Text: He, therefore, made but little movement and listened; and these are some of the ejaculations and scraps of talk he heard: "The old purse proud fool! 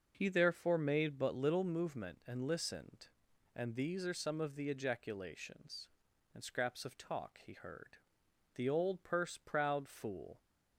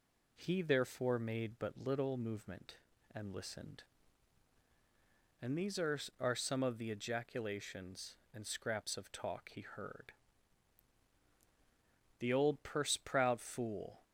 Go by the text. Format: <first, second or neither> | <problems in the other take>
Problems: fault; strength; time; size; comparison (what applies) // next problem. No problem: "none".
first | says "are" twice; at 6.2 s